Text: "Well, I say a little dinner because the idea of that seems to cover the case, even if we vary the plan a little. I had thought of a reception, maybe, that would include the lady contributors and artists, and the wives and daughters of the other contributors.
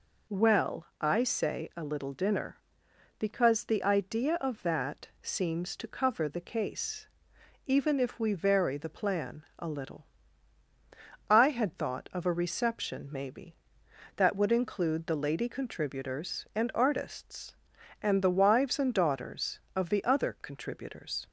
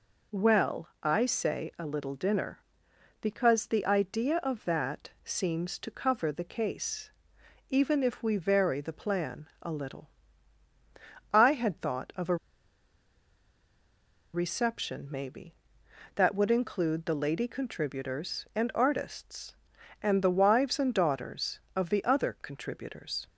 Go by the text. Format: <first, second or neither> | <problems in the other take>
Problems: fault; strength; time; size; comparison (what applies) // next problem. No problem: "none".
first | pauses between "a" and "reception"; strong; at 12.3 s; 1.9 s long